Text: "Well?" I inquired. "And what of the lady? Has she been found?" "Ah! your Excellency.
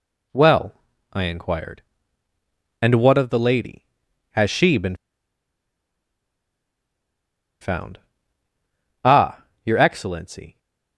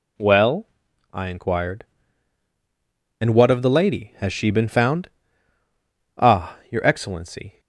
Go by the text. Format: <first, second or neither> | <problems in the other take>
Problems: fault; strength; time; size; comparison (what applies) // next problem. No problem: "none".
second | pauses between "been" and "found"; strong; at 4.9 s; 2.6 s long